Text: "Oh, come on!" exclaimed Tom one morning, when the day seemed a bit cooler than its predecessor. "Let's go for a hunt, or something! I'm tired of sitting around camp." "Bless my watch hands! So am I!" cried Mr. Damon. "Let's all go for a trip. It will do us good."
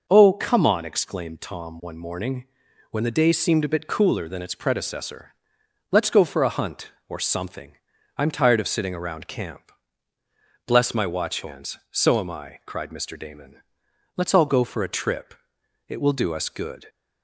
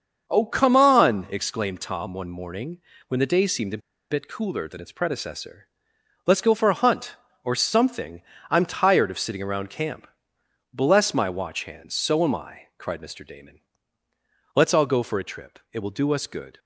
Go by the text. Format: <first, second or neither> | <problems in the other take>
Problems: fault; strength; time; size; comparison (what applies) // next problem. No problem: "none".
first | starts louder than the rest; until 1.3 s; 6.5 dB; noticeable in the first // pauses between "a" and "bit"; slight; at 3.8 s; 0.31 s long